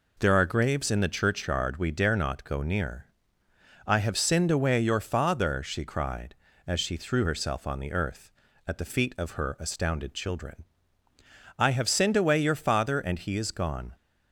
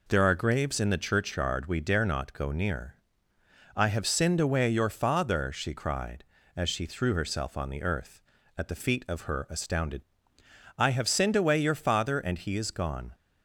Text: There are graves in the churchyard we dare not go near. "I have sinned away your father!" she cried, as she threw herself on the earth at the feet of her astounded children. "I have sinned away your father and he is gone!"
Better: first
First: none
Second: skips "children"; at 10.4 s

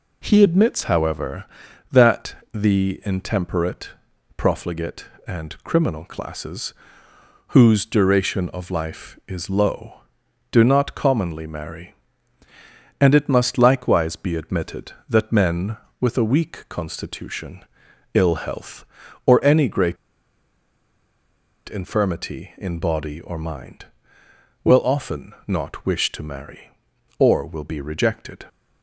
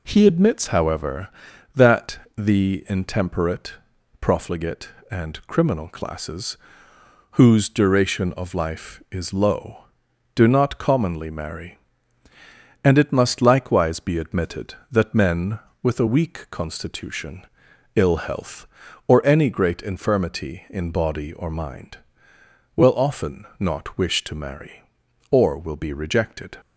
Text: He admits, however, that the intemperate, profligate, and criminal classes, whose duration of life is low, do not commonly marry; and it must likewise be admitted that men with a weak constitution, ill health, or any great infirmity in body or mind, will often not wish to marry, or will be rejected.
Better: second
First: pauses between "that" and "the"; slight; at 2.3 s; 0.18 s long // pauses between "great" and "infirmity"; strong; at 19.9 s; 1.7 s long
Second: pauses between "that" and "the"; slight; at 2.2 s; 0.18 s long

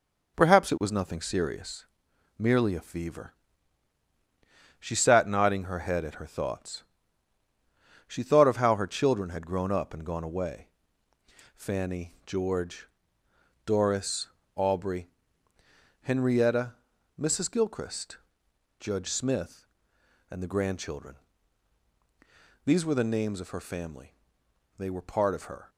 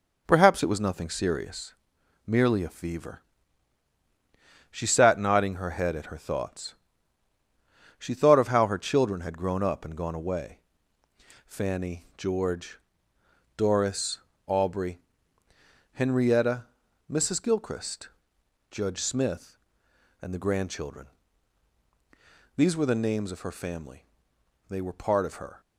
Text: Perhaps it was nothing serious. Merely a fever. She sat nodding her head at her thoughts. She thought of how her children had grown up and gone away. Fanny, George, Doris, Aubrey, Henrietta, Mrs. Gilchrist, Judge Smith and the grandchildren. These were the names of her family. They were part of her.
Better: neither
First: none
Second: none

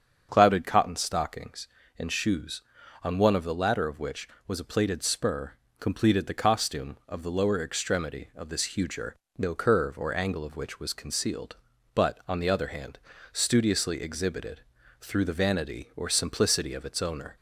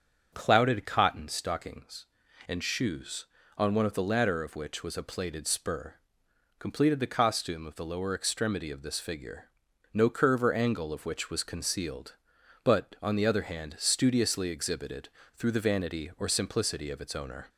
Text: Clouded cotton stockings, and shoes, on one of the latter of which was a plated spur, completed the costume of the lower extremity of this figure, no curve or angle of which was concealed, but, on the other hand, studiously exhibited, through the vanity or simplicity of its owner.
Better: second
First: starts louder than the rest; strong; until 1.3 s; 7 dB // says "huger" for "figure"; at 8.7 s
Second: starts louder than the rest; until 1.3 s; 7 dB

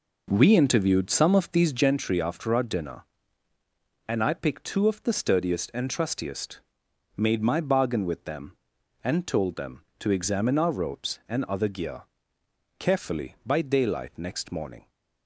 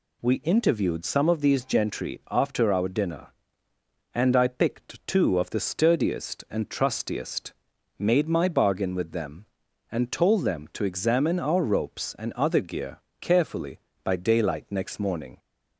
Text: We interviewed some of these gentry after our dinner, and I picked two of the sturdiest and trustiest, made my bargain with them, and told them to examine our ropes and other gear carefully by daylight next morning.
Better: second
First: starts louder than the rest; noticeable; until 2.1 s; 5 dB // pauses between "gear" and "carefully"; noticeable; at 12.0 s; 0.74 s long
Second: pauses between "gear" and "carefully"; slight; at 12.9 s; 0.22 s long

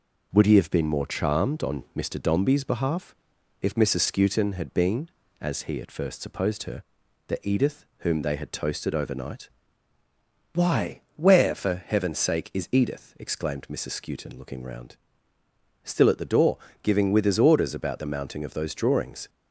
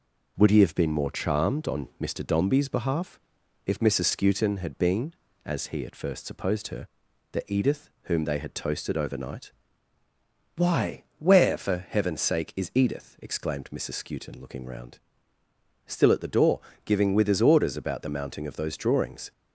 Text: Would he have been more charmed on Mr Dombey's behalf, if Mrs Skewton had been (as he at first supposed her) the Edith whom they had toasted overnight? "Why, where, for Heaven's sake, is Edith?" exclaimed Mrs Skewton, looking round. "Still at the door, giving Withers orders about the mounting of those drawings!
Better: neither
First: none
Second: none

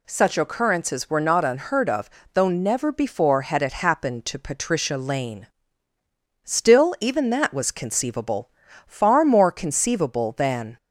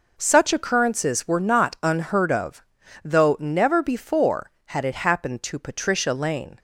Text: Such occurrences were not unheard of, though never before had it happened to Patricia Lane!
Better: second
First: goes on to say "Still even that was conceivable far more conceivable than"; strong; from 6.4 s on; 4.3 s long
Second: none

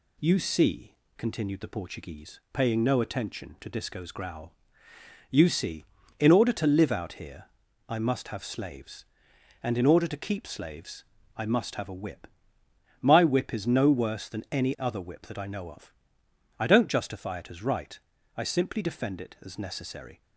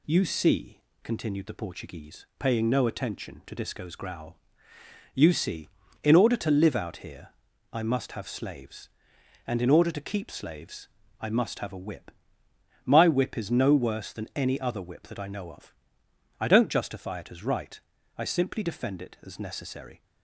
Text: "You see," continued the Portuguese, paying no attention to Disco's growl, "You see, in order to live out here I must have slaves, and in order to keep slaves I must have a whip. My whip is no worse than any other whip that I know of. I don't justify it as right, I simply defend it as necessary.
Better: neither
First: pauses between "here" and "I"; at 7.4 s; 0.42 s long // pauses between "slaves" and "I"; slight; at 11.0 s; 0.32 s long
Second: pauses between "here" and "I"; at 7.2 s; 0.42 s long // pauses between "slaves" and "I"; slight; at 10.8 s; 0.32 s long

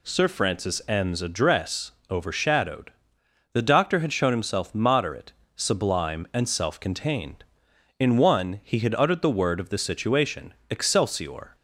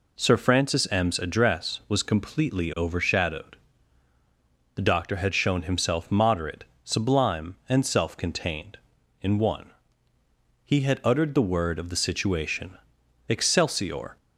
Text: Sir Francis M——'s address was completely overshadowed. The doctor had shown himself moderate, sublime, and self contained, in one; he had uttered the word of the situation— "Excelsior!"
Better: second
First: skips "was completely"; at 2.0 s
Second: none

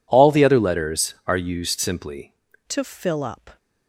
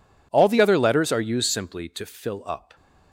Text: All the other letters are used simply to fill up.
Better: second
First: changes voice at "to"; from 2.6 s on; 0.9 s long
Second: none

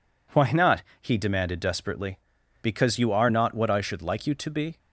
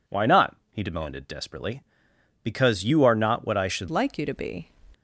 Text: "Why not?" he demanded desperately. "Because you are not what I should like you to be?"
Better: first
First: none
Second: changes voice at "like"; from 3.9 s on; 0.7 s long

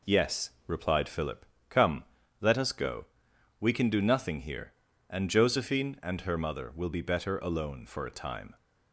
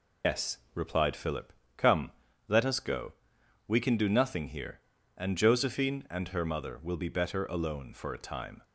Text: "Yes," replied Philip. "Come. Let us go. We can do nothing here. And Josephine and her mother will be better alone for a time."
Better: first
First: none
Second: loses the start of "Yes"; at 0.2 s; 130 ms

